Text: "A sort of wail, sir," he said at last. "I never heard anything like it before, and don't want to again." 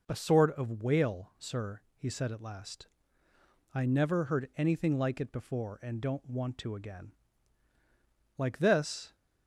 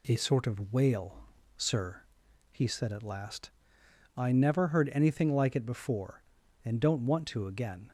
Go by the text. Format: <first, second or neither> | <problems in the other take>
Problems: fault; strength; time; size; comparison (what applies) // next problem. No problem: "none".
second | goes on to say "Like this"; noticeable; from 8.3 s on; 0.78 s long